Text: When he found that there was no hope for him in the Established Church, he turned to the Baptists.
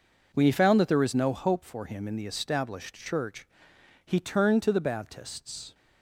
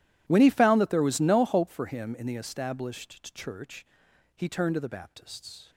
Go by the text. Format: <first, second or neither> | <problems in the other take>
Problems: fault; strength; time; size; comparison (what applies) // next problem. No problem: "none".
first | gets quieter; strong; throughout; 20.5 dB